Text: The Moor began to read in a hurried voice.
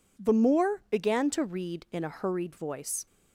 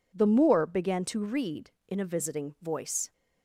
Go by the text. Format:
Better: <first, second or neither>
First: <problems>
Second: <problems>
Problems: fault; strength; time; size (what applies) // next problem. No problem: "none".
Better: first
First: none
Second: says "visiting" for "hurried"; at 2.0 s